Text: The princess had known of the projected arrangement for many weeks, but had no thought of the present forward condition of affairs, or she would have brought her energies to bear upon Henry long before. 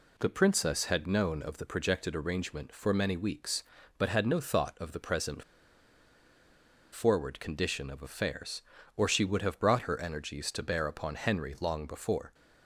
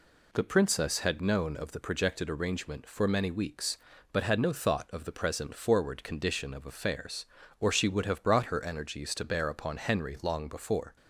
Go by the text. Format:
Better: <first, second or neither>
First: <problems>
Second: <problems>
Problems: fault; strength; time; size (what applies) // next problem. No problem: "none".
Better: second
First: pauses between "present" and "forward"; strong; at 5.4 s; 1.4 s long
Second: none